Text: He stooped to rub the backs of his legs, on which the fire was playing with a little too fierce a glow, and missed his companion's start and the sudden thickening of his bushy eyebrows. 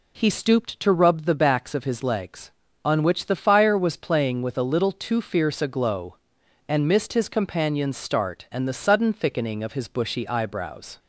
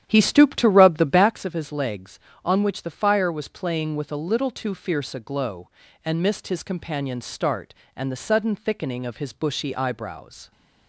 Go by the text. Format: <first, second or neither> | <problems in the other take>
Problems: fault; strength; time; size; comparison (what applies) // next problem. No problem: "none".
first | starts louder than the rest; strong; until 1.4 s; 10.5 dB